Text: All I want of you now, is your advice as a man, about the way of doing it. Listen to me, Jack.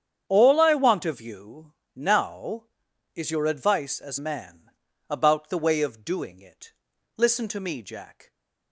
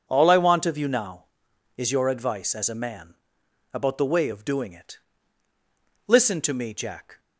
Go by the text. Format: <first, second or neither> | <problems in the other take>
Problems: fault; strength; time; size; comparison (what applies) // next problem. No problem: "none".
second | starts louder than the rest; strong; until 1.2 s; 8.5 dB // pauses between "you" and "now"; slight; at 1.7 s; 0.20 s long // skips "a"; at 4.1 s